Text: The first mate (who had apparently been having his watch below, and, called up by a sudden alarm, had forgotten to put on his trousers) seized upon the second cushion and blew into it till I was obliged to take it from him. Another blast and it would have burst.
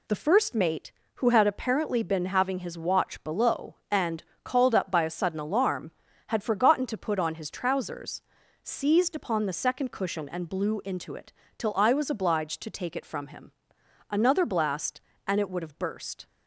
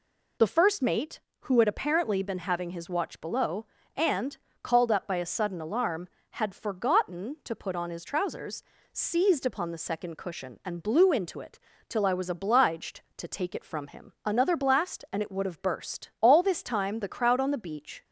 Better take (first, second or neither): first